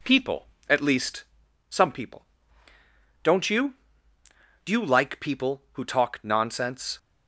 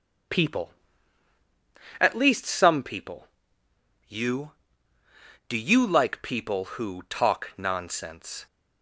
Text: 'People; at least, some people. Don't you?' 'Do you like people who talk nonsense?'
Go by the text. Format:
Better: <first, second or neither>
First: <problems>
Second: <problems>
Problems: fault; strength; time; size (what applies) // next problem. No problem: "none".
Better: first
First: none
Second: skips "Don't"; at 3.6 s